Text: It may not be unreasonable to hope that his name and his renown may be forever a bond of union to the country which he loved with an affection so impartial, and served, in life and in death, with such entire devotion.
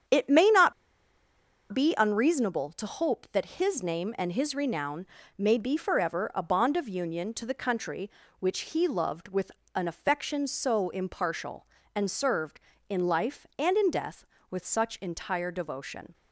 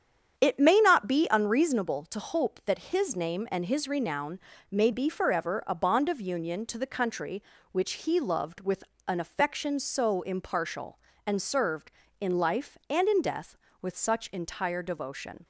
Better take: second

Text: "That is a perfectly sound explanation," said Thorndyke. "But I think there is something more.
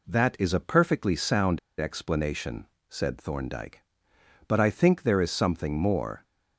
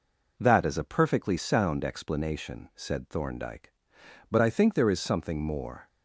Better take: second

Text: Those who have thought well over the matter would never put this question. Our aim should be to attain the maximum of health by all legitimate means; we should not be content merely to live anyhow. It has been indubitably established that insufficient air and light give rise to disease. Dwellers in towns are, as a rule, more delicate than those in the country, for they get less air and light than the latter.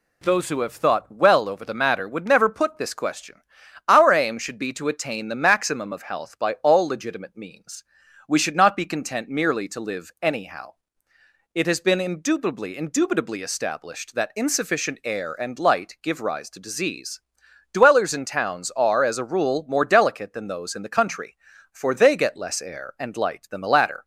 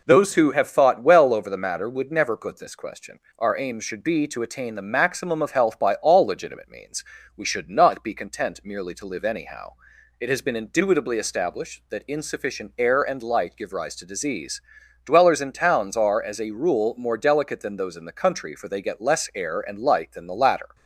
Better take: second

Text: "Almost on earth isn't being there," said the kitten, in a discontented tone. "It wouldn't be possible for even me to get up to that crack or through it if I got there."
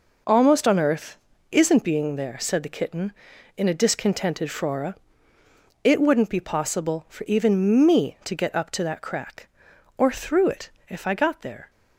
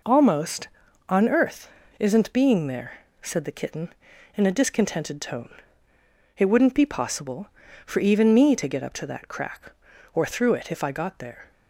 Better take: second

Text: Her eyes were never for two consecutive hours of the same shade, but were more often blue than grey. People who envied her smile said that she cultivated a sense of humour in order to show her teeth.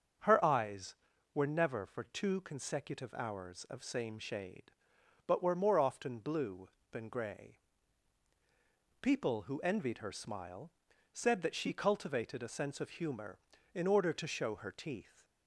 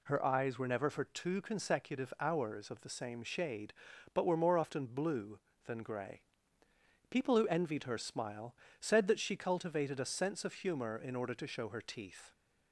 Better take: second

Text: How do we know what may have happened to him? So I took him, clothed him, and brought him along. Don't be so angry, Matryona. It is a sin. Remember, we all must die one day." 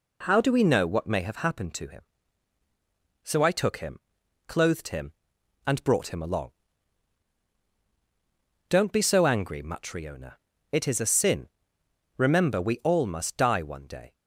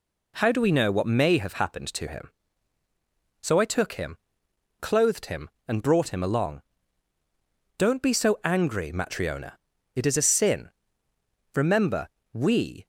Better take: first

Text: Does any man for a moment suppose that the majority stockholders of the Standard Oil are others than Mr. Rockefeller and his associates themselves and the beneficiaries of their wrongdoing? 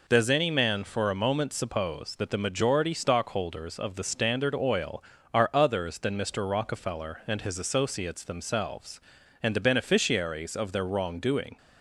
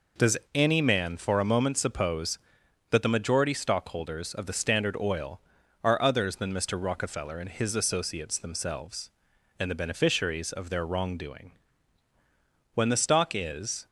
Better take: first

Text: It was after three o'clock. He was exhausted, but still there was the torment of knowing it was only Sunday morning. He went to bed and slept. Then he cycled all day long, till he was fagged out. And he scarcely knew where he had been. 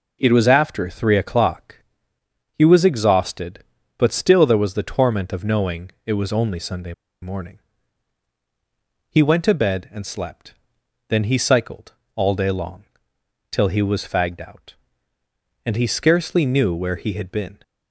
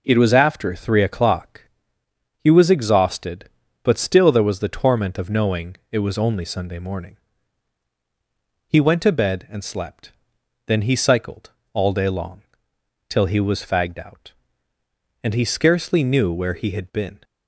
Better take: second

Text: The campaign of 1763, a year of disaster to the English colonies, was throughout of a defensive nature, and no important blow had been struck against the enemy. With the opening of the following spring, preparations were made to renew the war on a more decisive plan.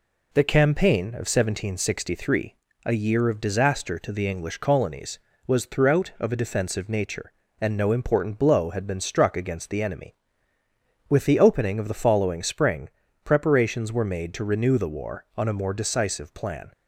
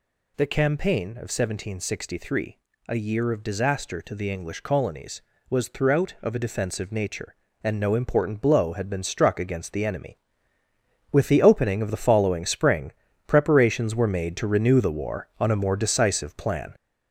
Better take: first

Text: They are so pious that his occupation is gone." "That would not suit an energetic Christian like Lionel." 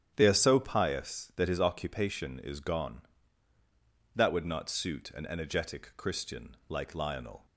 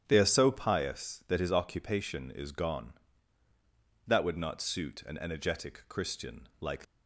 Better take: first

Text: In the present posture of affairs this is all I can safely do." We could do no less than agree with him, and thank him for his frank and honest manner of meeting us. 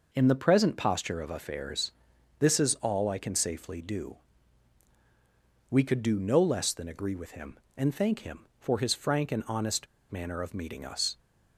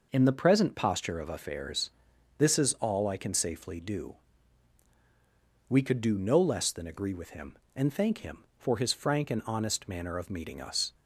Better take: second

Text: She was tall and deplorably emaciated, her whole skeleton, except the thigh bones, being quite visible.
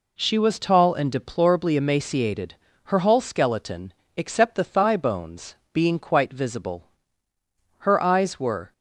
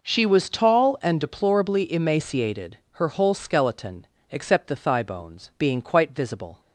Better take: second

